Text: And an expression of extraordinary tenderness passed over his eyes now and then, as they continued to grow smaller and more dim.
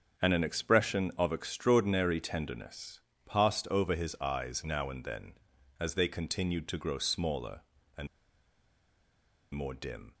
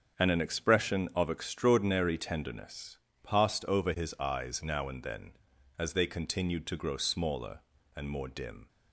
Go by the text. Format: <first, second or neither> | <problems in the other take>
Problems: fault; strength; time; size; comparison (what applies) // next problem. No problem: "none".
second | starts louder than the rest; strong; until 1.2 s; 7 dB; strong in the second // pauses between "tenderness" and "passed"; slight; at 3.0 s; 0.28 s long; slight in the second // pauses between "and" and "more"; strong; at 8.0 s; 1.4 s long